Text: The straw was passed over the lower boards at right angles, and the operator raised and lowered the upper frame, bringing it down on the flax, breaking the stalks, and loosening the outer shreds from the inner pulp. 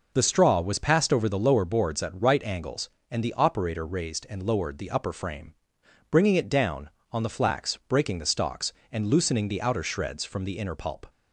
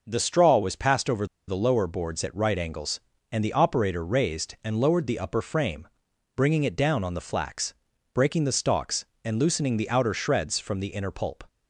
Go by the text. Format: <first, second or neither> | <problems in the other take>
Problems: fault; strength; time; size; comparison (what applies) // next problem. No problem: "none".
first | pauses between "over" and "the"; slight; at 1.2 s; 0.21 s long